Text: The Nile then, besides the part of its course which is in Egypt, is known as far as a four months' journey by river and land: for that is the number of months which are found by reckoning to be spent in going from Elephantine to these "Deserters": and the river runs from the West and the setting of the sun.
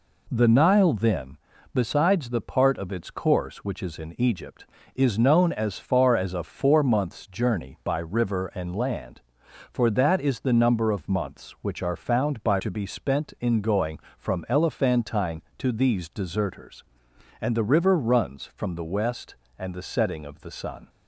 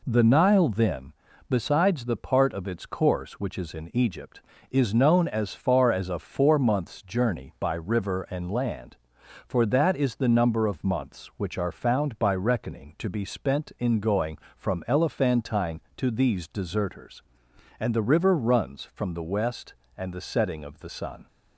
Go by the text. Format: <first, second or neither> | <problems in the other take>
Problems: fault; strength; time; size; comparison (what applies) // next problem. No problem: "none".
second | skips "reckoning"; at 12.5 s